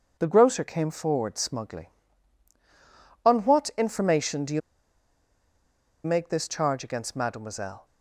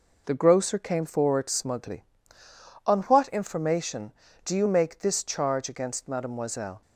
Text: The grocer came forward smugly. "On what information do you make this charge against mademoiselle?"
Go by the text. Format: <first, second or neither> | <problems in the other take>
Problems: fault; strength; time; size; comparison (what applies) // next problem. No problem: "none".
second | pauses between "you" and "make"; strong; at 4.6 s; 1.4 s long